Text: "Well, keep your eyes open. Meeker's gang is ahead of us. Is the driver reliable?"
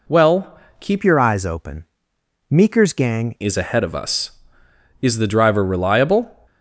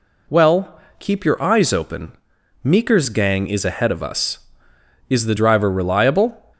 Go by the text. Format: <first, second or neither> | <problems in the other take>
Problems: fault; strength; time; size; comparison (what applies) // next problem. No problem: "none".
second | changes voice from "your" to "gang"; from 1.0 to 3.3 s; 2.3 s long